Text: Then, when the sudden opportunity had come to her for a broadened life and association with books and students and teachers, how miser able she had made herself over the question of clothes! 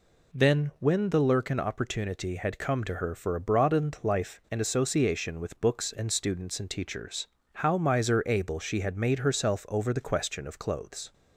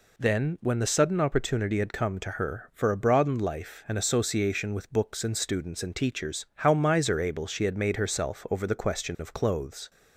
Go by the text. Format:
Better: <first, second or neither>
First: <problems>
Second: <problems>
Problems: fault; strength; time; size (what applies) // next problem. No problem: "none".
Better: second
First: says "lurkin" for "sudden"; at 1.1 s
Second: none